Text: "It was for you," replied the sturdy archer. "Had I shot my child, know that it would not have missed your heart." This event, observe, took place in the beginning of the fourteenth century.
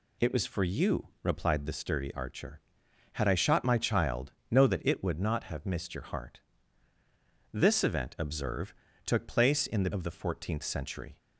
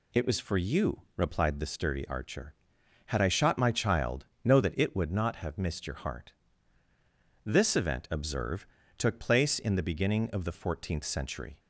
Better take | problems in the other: second | skips "beginning"; at 9.9 s

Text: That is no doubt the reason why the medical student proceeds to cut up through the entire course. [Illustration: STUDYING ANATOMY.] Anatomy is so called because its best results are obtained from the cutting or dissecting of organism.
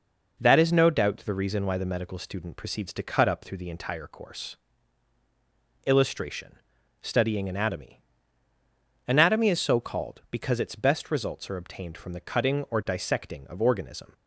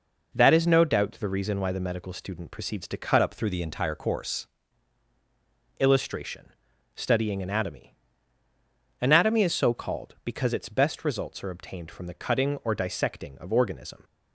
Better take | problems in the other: first | changes voice from "up" to "course"; from 3.2 to 4.4 s; 1.2 s long

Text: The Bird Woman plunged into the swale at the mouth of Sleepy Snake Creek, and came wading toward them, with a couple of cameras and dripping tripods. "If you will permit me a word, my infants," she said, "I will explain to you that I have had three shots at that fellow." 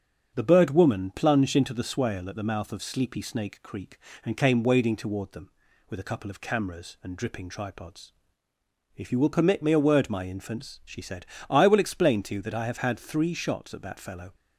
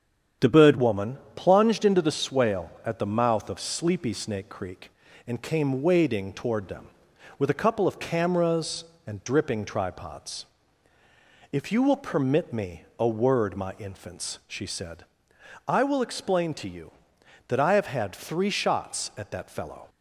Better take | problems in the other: first | starts louder than the rest; strong; until 1.6 s; 8.5 dB; strong in the first // changes voice at "Woman"; from 0.7 s on; 19.1 s long // pauses between "Woman" and "plunged"; slight; at 1.1 s; 0.18 s long

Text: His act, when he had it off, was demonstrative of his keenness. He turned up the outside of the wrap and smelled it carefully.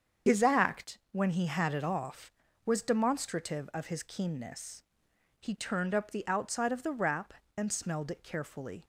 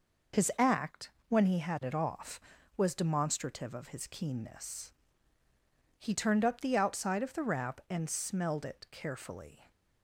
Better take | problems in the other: second | loses the start of "His"; at 0.2 s; 65 ms // starts louder than the rest; strong; until 1.4 s; 7 dB

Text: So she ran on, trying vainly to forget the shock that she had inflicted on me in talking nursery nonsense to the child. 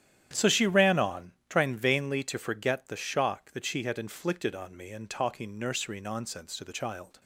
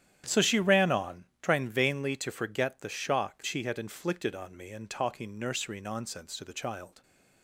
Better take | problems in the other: first | starts louder than the rest; strong; until 1.4 s; 10.5 dB; strong in the first // skips "that"; at 3.4 s

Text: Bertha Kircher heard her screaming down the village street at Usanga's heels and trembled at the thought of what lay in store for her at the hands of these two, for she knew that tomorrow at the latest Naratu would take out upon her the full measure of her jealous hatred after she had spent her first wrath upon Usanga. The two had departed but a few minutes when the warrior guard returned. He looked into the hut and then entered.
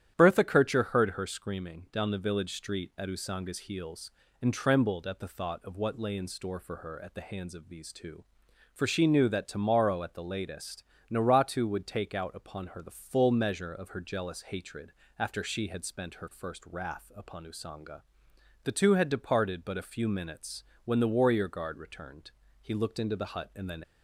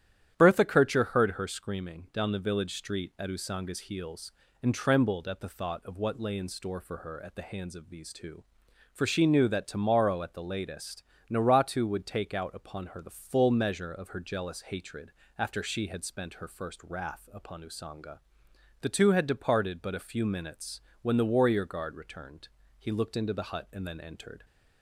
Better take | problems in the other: second | starts louder than the rest; strong; until 1.2 s; 10.5 dB; strong in the second // pauses between "latest" and "Naratu"; slight; at 10.8 s; 0.28 s long; slight in the second // pauses between "hatred" and "after"; slight; at 14.9 s; 0.26 s long; slight in the second // pauses between "minutes" and "when"; slight; at 20.6 s; 0.22 s long; slight in the second // stops before "entered"; at 23.8 s

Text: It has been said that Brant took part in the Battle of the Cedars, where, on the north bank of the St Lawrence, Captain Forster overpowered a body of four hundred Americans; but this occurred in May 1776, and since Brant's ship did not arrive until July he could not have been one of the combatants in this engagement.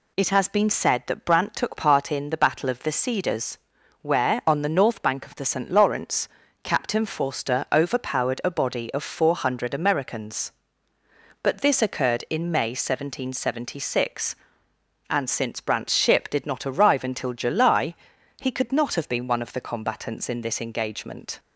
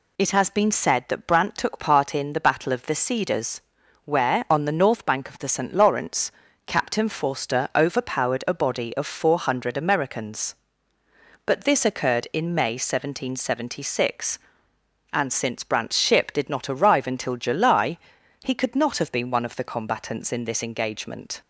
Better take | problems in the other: neither | pauses between "July" and "he"; noticeable; the same in both

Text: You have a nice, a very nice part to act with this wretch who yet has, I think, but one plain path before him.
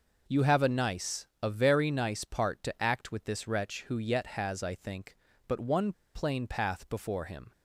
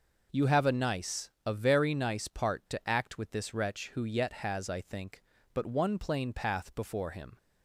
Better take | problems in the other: second | pauses between "one" and "plain"; slight; at 5.9 s; 0.22 s long

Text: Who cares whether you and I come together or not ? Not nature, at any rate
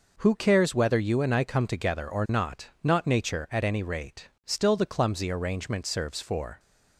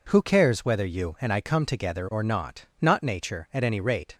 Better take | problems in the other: second | goes on to say "Still the clumsy arrangement serves for"; strong; from 4.4 s on; 2.1 s long

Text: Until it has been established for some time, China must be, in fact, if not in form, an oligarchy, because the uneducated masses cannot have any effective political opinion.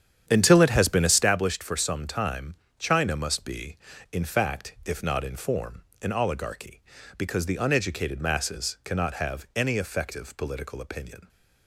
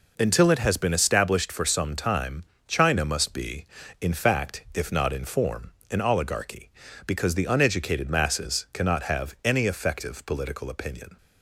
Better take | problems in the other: second | starts louder than the rest; strong; until 1.3 s; 9 dB

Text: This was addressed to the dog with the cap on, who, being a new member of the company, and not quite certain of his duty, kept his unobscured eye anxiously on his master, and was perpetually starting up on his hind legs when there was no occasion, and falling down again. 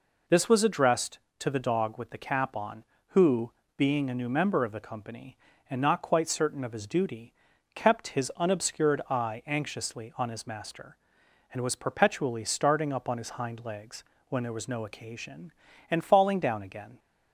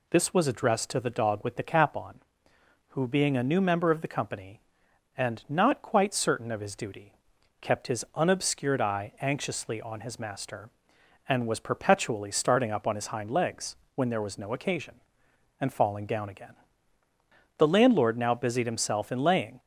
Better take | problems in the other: first | pauses between "legs" and "when"; slight; at 13.7 s; 0.20 s long; slight in the first // goes on to say "The landlord now busied himself in laying"; strong; from 17.5 s on; 2.0 s long

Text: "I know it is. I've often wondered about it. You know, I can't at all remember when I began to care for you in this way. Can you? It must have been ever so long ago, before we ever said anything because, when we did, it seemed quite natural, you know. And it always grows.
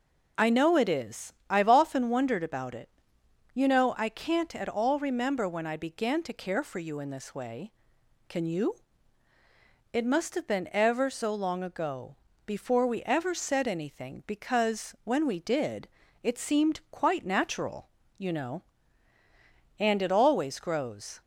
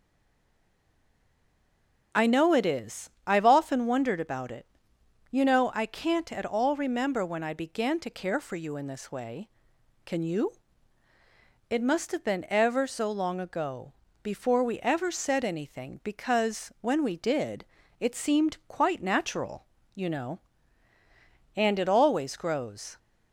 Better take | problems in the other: first | stays silent before the first word; until 2.1 s; 2.1 s long

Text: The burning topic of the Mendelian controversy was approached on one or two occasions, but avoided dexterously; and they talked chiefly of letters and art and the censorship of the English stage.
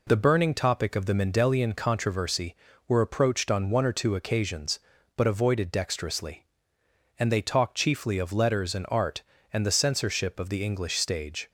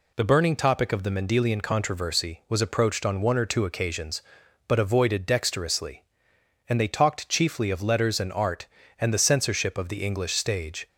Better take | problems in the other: second | says "were" for "was"; at 2.8 s

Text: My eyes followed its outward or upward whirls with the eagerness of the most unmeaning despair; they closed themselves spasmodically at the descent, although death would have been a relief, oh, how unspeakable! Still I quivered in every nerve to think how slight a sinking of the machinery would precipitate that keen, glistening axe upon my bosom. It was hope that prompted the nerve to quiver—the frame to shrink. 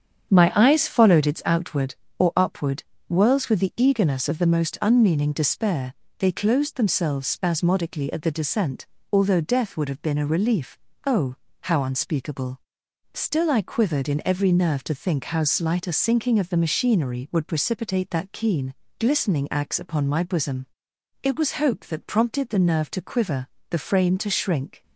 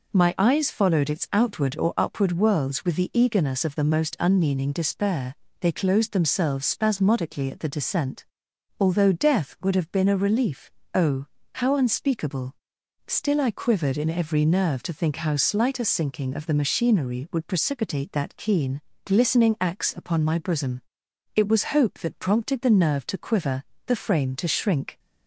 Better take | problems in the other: second | starts louder than the rest; strong; until 1.5 s; 8 dB // pauses between "upward" and "whirls"; slight; at 2.8 s; 0.24 s long

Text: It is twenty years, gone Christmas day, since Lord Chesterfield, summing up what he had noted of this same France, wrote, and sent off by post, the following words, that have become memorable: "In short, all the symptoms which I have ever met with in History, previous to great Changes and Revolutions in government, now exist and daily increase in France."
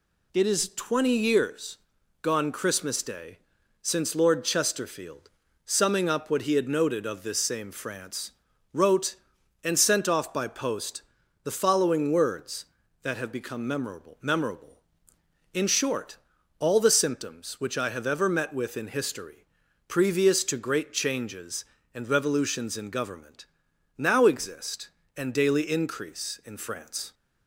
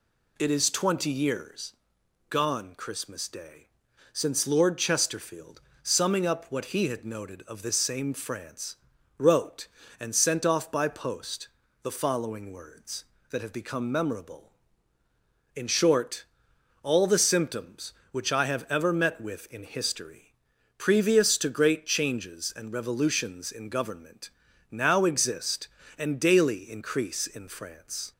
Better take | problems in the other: second | says "memorable" twice; at 14.2 s

